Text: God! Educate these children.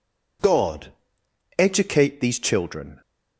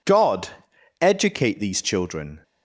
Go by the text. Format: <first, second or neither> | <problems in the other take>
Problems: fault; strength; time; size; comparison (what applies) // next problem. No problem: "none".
neither | none